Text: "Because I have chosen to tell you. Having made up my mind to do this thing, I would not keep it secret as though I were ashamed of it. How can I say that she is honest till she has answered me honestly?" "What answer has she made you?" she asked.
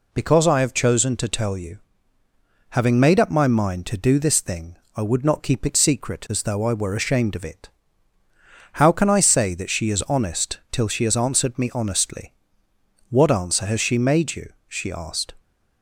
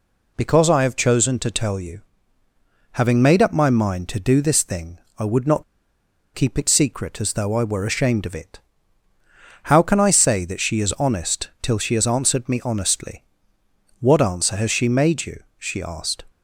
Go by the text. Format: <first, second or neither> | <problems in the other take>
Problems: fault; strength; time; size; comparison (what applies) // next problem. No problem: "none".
first | pauses between "not" and "keep"; noticeable; at 5.6 s; 0.72 s long